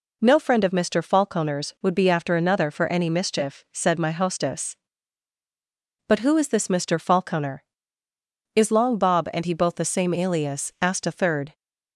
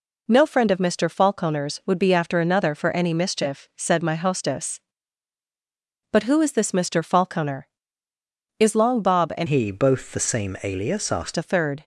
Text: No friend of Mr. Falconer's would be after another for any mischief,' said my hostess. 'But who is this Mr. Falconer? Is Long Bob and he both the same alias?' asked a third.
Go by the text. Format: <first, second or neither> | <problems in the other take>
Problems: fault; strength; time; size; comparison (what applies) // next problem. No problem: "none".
first | changes voice from "he" to "asked"; from 9.4 to 11.3 s; 1.9 s long